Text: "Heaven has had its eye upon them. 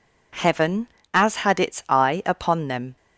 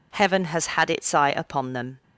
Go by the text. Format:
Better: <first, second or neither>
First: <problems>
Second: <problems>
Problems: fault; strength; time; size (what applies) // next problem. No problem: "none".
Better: second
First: says "as" for "has"; at 1.1 s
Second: none